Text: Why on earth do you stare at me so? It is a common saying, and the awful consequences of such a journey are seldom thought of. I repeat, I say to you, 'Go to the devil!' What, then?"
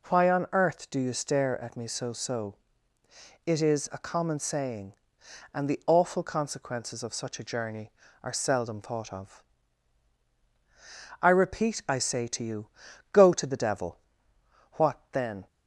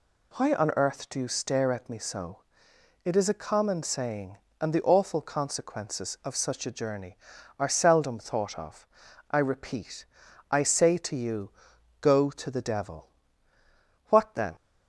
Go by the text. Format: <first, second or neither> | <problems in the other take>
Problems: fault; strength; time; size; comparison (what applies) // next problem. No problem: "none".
second | says "so" twice; at 2.1 s